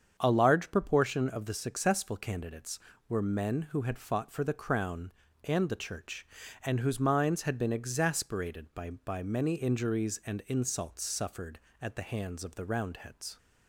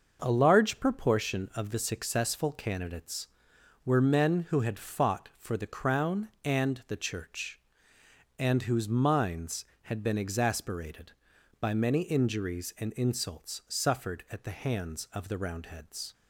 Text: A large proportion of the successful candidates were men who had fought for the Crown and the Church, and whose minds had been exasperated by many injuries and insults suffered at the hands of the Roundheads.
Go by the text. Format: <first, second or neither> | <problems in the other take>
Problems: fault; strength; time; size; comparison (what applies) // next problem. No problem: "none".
second | starts louder than the rest; strong; until 1.1 s; 7.5 dB; noticeable in the second // says "by" twice; at 8.8 s